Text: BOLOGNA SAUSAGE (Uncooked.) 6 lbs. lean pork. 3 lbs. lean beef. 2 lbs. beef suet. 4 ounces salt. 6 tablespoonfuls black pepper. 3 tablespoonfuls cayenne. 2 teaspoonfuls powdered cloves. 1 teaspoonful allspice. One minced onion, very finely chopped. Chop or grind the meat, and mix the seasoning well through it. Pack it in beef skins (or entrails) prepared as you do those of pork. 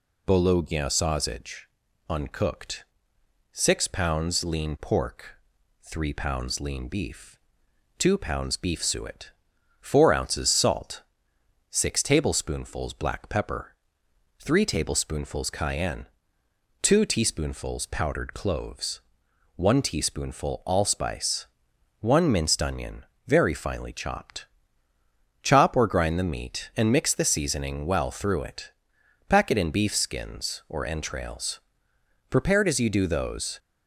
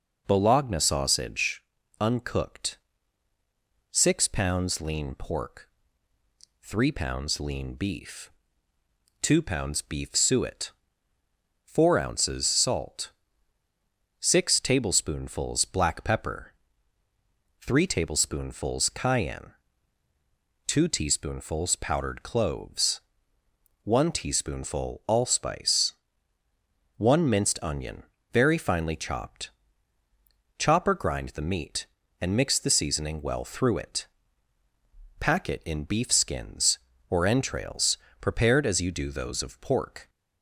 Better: second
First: stops before "of pork"; at 33.5 s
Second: none

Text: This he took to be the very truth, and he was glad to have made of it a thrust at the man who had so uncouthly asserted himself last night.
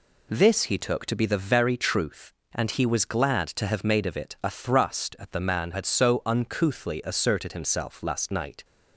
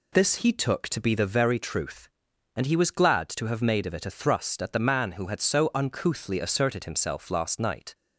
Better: second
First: skips "who"; at 5.7 s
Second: none

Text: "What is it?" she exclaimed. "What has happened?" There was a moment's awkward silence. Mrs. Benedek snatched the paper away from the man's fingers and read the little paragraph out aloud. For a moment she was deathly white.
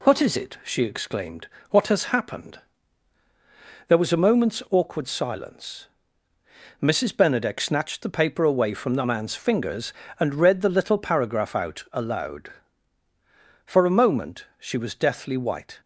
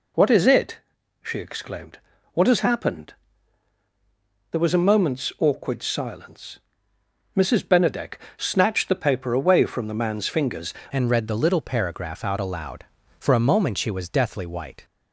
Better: first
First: none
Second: pauses between "Benedek" and "snatched"; slight; at 8.1 s; 0.20 s long // changes voice at "and"; from 10.9 s on; 3.9 s long

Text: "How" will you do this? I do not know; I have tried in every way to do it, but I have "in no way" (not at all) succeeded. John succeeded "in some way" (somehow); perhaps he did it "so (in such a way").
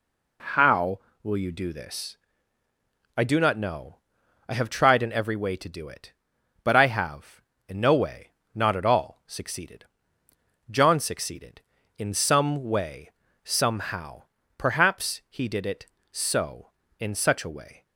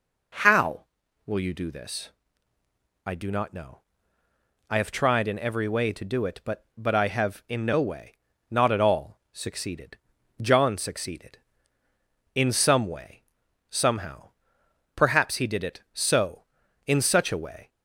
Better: first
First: none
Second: says "but" twice; at 6.7 s

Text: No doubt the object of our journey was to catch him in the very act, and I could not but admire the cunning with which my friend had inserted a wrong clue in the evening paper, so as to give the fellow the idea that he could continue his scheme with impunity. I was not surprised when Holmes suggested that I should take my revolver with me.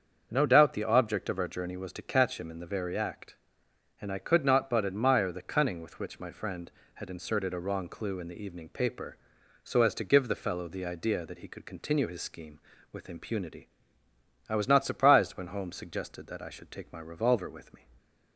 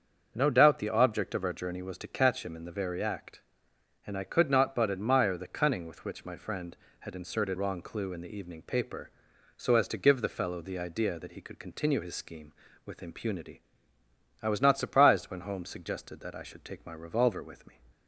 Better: first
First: starts louder than the rest; until 1.3 s; 7 dB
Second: starts louder than the rest; until 1.3 s; 7 dB // skips "a"; at 7.5 s

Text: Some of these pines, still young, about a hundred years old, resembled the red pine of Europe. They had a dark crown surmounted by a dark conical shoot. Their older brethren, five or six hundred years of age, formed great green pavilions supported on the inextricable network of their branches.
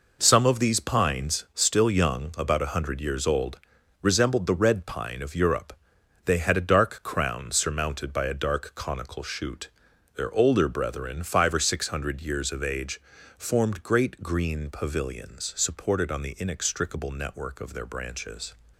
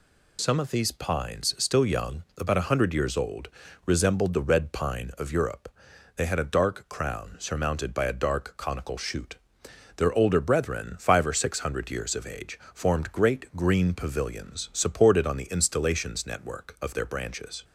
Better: first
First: none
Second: says "installations" for "inextricable"; at 15.5 s

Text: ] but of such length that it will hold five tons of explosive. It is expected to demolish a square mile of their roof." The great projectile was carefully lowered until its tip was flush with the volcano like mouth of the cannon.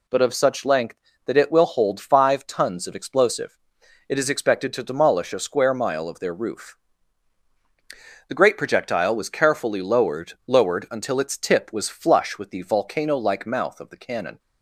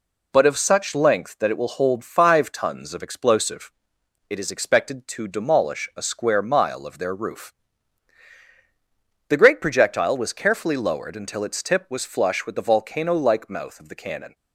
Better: second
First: says "lowered" twice; at 10.4 s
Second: none

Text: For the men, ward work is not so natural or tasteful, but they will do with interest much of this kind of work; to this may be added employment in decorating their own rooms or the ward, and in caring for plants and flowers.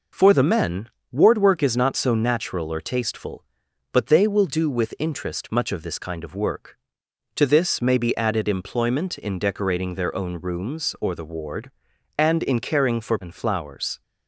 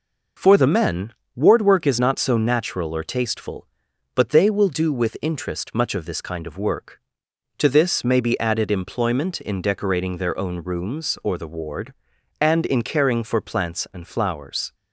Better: second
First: skips "plants"; at 13.1 s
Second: none

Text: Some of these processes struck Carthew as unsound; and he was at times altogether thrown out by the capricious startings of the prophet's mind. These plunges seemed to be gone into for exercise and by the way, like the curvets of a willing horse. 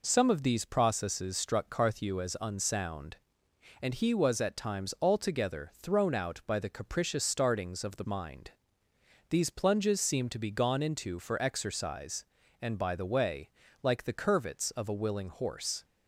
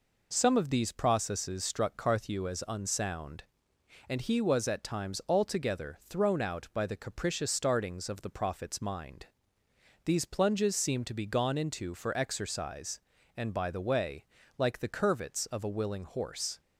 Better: second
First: skips "prophet's"; at 8.0 s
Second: none

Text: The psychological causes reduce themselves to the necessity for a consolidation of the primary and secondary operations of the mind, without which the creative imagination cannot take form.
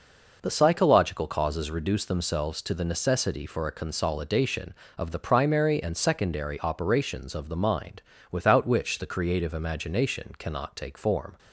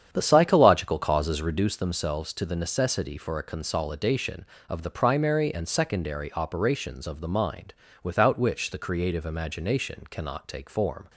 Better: first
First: none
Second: starts louder than the rest; strong; until 1.7 s; 8.5 dB

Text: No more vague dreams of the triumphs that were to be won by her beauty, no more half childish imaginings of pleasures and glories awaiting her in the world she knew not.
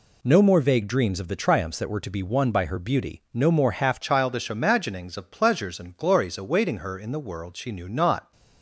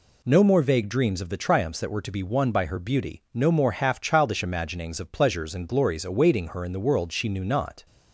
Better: second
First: changes voice at "childish"; from 4.0 s on; 4.3 s long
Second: none

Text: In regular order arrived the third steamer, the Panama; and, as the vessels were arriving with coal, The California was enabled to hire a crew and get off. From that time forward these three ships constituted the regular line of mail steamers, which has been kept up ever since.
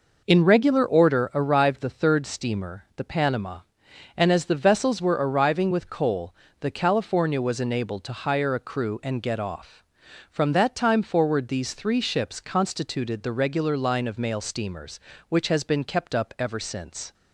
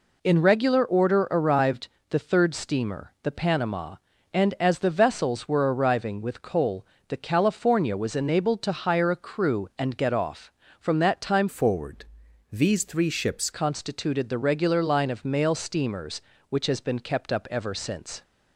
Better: first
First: none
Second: pauses between "arrived" and "the"; slight; at 1.8 s; 0.22 s long // changes voice from "forward" to "ships"; from 11.4 to 13.4 s; 2.0 s long // pauses between "forward" and "these"; noticeable; at 12.0 s; 0.48 s long

